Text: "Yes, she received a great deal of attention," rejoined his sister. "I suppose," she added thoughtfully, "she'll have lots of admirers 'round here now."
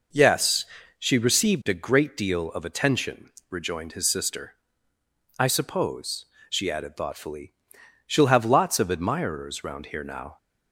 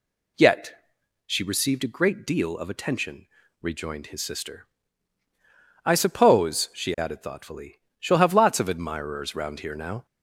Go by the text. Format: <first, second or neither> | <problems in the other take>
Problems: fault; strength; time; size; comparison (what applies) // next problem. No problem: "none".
first | says "Yet" for "Yes"; at 0.3 s